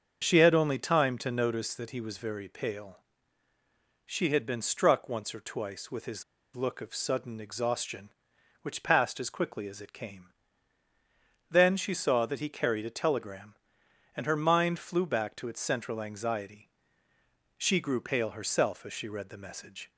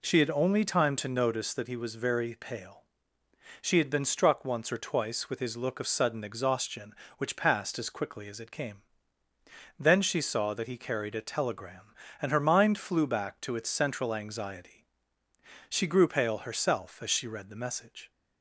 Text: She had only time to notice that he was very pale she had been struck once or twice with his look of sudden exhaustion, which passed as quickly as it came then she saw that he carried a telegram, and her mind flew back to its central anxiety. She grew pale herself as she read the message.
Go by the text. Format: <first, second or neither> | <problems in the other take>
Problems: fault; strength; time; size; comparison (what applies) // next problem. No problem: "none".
second | starts louder than the rest; until 1.2 s; 6.5 dB // pauses between "pale" and "she"; at 2.9 s; 1.0 s long; noticeable in the second // pauses between "his" and "look"; slight; at 6.2 s; 0.31 s long // pauses between "came" and "then"; at 10.2 s; 1.2 s long; noticeable in the second